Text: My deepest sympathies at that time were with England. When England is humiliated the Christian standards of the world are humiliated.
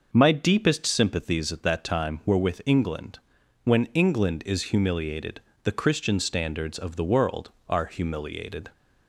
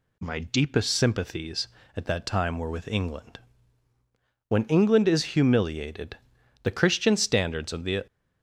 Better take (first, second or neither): first